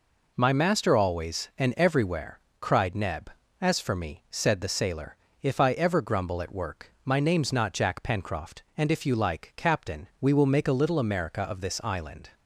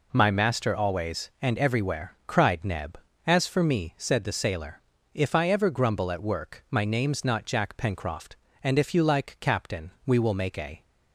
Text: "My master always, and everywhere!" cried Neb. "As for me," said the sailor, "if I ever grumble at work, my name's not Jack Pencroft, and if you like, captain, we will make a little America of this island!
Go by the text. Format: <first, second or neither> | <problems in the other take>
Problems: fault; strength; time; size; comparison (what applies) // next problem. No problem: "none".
first | stops before "little America of this island"; at 10.8 s